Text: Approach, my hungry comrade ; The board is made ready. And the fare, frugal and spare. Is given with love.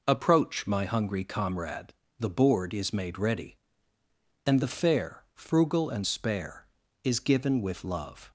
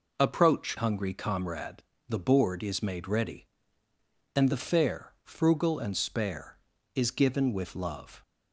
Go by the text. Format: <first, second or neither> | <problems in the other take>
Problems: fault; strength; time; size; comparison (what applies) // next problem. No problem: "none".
first | skips "my"; at 0.7 s